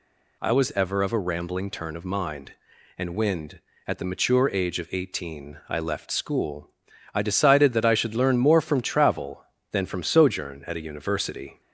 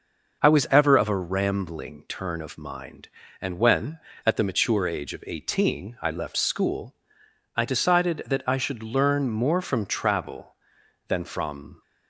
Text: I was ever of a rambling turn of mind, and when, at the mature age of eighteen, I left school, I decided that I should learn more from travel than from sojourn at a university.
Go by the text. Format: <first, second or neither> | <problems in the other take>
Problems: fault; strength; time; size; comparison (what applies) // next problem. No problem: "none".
first | stops before "sojourn at a university"; at 11.8 s